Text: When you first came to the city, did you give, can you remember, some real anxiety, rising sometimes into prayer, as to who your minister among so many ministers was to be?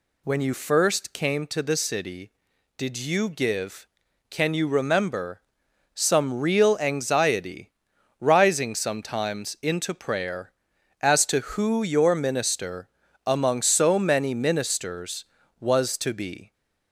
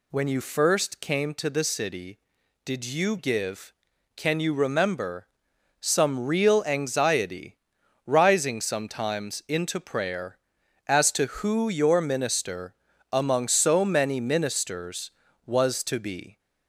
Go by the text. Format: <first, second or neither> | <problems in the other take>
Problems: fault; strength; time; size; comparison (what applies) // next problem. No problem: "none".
neither | pauses between "minister" and "among"; the same in both